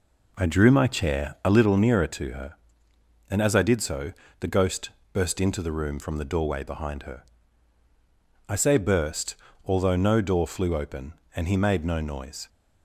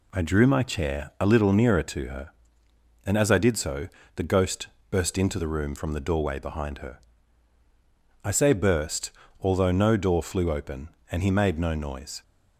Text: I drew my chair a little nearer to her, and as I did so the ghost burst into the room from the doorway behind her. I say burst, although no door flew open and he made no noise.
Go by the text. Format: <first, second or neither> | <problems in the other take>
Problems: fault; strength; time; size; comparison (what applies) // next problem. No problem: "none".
second | starts louder than the rest; until 1.7 s; 3.5 dB // pauses between "so" and "the"; slight; at 4.1 s; 0.28 s long; slight in the second // pauses between "ghost" and "burst"; slight; at 4.8 s; 0.24 s long; slight in the second